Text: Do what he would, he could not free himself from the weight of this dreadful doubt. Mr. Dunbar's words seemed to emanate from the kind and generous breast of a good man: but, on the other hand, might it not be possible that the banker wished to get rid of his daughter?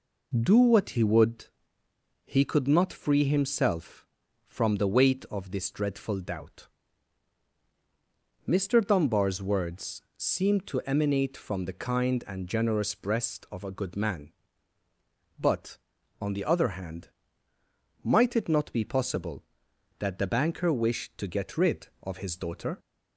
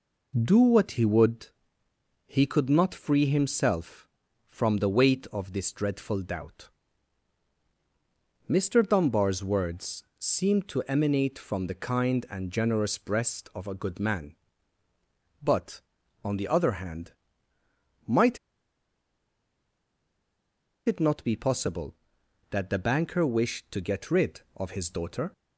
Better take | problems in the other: first | pauses between "words" and "seemed"; slight; at 10.0 s; 0.16 s long; slight in the first // pauses between "might" and "it"; strong; at 18.3 s; 2.5 s long

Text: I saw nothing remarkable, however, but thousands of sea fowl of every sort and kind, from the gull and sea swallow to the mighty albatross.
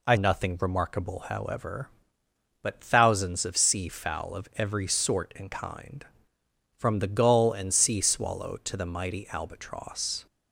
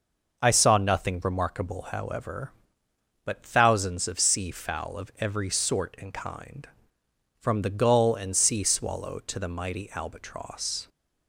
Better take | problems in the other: second | skips "saw"; at 0.1 s

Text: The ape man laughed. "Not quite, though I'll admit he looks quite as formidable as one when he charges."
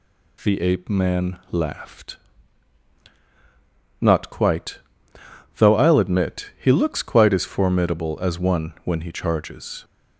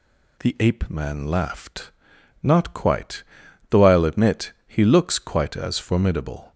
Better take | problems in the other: first | pauses between "admit" and "he"; slight; at 4.5 s; 0.16 s long // stops before "as one when he charges"; at 6.5 s

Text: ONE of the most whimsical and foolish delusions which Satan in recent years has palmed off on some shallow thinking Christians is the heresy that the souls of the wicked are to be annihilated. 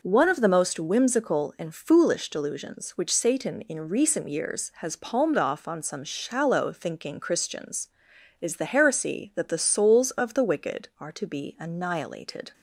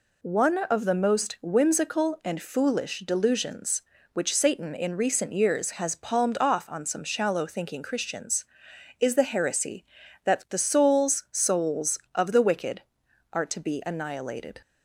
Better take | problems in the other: first | says "souls" twice; at 11.3 s

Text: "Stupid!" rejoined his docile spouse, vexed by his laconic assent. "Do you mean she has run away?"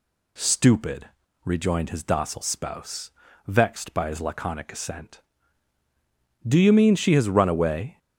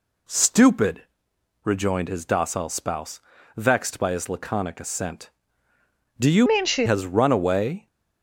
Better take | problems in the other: first | changes voice from "mean" to "she"; from 6.4 to 6.8 s; 0.4 s long

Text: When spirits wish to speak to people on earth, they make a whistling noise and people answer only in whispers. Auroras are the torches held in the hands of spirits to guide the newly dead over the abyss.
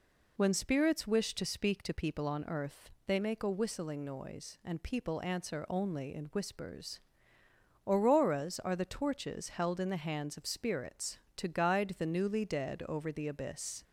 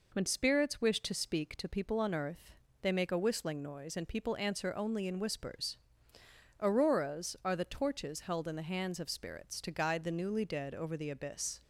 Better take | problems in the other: neither | none

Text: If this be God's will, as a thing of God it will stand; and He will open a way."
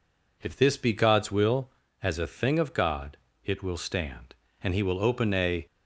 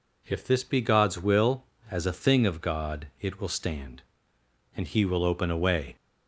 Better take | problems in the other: second | pauses between "God" and "it"; slight; at 3.1 s; 0.26 s long // stops before "way"; at 5.6 s

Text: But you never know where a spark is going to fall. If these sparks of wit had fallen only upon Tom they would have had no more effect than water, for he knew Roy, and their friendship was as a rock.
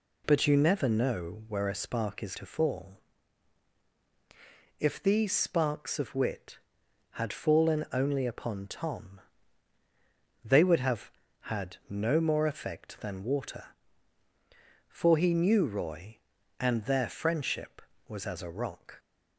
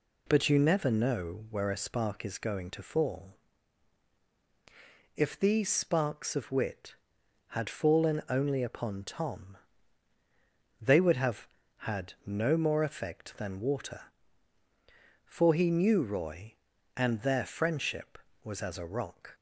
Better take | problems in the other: second | skips "going"; at 2.3 s // pauses between "Tom" and "they"; at 9.1 s; 1.2 s long; also in the second

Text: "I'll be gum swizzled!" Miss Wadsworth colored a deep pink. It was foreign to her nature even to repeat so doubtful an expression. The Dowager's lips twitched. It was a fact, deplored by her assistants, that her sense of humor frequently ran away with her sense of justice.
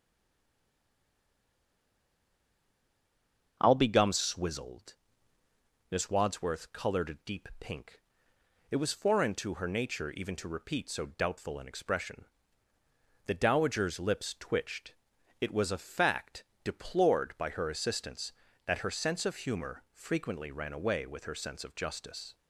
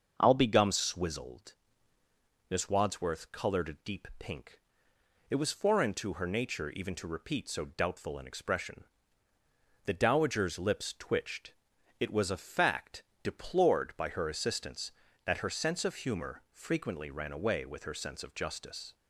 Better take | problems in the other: second | stays silent before the first word; strong; until 3.5 s; 3.5 s long // starts louder than the rest; until 4.6 s; 6.5 dB; also in the second

